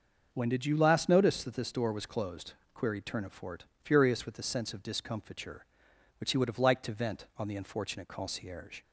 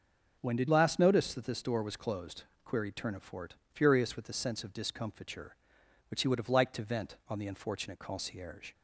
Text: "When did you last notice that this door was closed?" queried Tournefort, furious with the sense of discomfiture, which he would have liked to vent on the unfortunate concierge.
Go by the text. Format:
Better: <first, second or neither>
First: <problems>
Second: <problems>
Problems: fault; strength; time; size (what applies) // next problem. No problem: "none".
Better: first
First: starts louder than the rest; until 1.3 s; 6.5 dB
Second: starts louder than the rest; noticeable; until 1.4 s; 6 dB // skips "you"; at 0.6 s